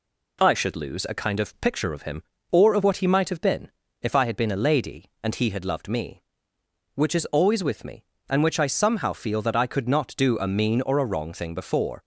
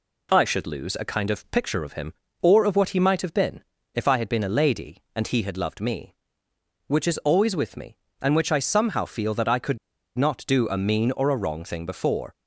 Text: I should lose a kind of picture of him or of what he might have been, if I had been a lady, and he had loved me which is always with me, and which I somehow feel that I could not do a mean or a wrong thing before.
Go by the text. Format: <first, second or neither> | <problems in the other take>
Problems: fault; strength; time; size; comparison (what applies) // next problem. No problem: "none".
first | pauses between "could" and "not"; at 9.7 s; 0.39 s long